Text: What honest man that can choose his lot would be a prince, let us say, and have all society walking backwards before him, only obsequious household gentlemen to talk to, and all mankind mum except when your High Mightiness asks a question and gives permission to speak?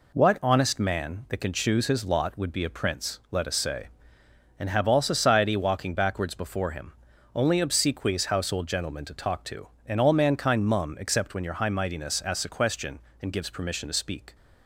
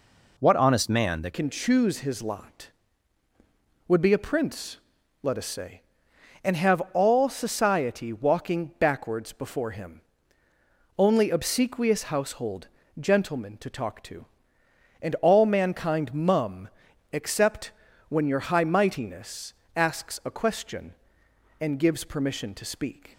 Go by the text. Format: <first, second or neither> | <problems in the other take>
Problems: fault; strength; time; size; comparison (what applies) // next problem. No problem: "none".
first | changes voice at "can"; from 1.3 s on; 21.8 s long // pauses between "household" and "gentlemen"; slight; at 12.6 s; 0.32 s long // pauses between "mum" and "except"; at 16.6 s; 0.44 s long // pauses between "except" and "when"; at 17.7 s; 0.40 s long // pauses between "Mightiness" and "asks"; slight; at 19.5 s; 0.20 s long